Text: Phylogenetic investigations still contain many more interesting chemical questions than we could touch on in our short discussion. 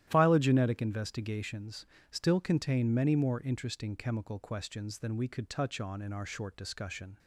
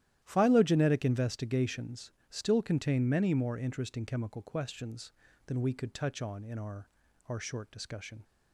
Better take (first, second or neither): first